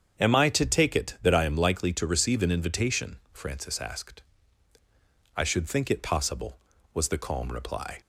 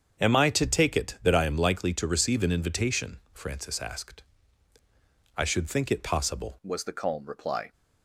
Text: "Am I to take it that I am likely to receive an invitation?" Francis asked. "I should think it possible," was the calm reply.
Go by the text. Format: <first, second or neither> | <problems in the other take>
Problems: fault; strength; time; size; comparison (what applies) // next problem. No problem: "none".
first | starts louder than the rest; strong; until 1.2 s; 7.5 dB; strong in the first // changes voice at "was"; from 6.6 s on; 1.1 s long